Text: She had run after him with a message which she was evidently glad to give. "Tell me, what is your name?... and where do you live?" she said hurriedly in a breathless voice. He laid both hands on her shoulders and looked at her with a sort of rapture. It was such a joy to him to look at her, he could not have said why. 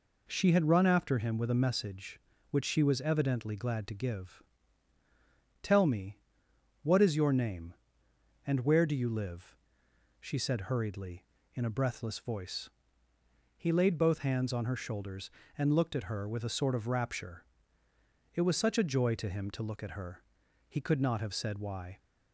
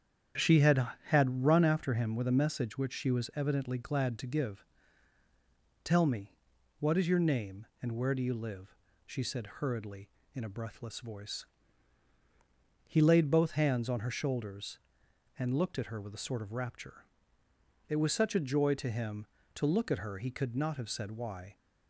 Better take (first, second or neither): first